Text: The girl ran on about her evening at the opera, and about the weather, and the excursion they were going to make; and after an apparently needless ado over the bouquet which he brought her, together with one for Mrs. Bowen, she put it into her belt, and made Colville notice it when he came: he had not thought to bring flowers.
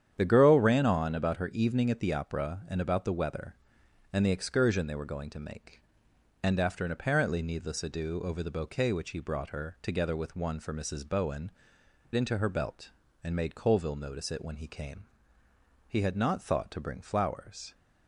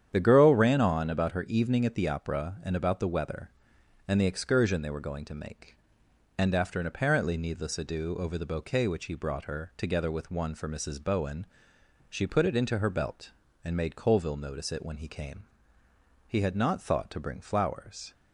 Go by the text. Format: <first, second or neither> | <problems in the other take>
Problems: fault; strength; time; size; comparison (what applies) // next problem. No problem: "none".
second | starts louder than the rest; strong; until 1.1 s; 9 dB; strong in the second // skips "she put it"; at 11.8 s